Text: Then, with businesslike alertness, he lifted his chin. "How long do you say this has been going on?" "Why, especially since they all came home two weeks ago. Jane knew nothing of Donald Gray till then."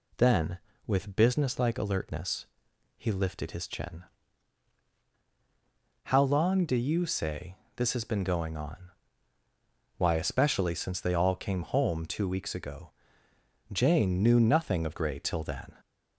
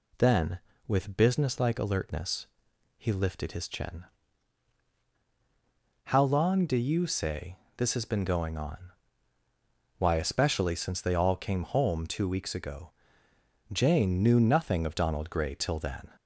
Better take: second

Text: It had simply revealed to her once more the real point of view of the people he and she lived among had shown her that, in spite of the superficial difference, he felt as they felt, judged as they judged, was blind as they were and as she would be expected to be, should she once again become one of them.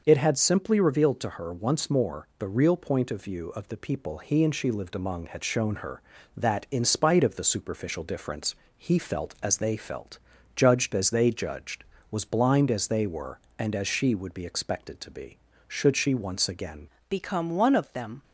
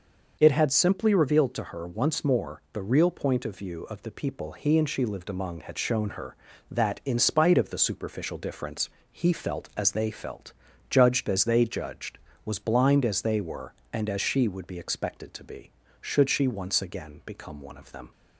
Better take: second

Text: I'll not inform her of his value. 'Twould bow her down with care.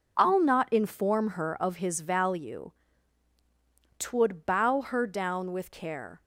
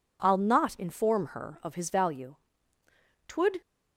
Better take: first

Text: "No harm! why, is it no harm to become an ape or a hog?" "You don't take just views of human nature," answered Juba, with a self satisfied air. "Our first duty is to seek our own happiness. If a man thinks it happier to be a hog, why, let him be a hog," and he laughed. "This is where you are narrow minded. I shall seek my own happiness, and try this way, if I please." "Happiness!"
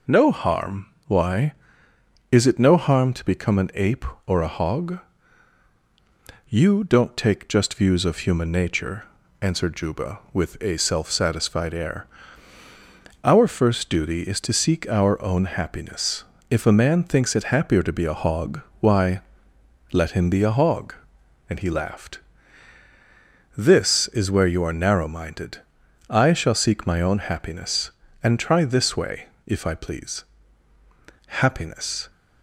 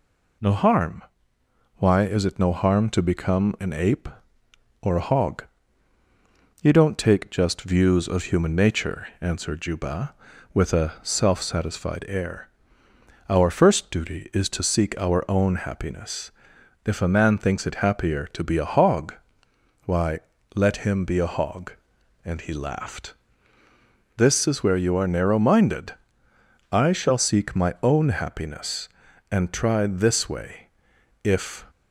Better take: first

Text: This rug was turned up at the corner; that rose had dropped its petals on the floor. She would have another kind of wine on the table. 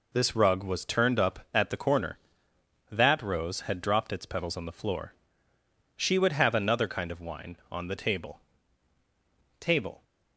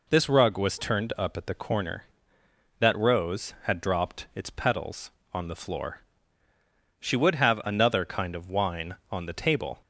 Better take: second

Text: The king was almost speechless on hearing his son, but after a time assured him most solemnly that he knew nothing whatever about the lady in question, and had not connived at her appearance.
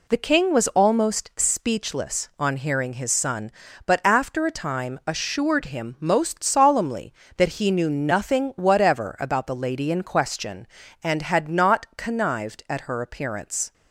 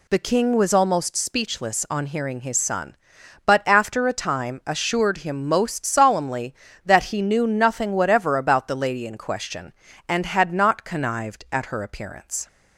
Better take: neither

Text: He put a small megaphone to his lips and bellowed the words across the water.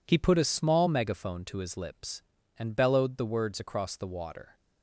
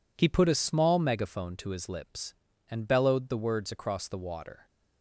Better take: neither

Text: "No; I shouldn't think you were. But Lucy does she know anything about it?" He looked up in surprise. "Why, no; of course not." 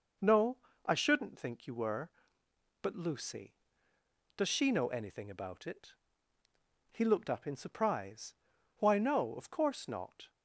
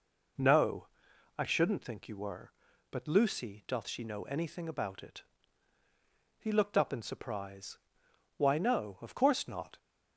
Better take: first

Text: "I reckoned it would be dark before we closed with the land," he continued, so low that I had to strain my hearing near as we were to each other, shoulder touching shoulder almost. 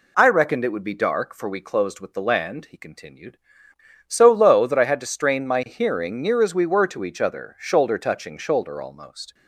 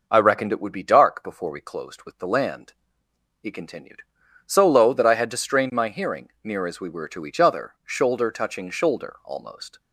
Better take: second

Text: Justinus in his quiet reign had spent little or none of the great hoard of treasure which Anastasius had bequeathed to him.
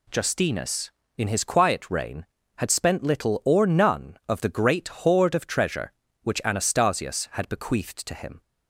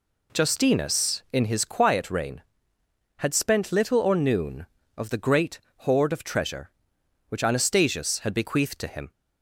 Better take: first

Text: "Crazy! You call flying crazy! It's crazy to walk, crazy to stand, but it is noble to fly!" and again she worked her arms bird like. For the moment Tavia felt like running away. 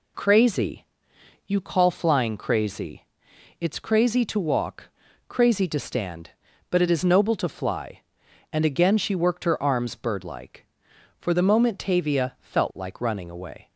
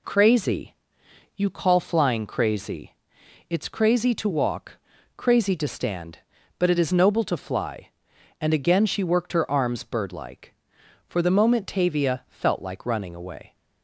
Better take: neither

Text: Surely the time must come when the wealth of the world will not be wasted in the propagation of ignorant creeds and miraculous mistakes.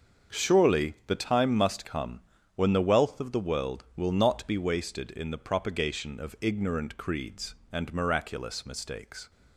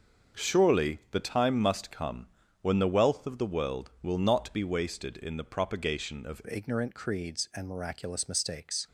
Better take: first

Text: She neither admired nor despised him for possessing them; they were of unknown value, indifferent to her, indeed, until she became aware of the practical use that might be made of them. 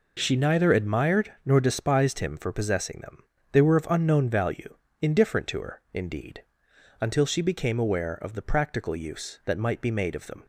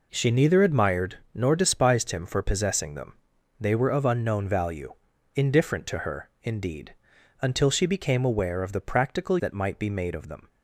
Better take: first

